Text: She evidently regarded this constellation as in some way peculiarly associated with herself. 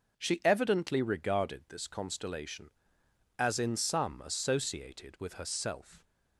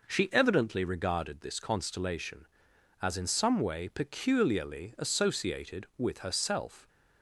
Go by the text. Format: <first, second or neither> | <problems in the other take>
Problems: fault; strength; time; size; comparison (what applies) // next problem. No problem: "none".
second | skips "way peculiarly"; at 4.2 s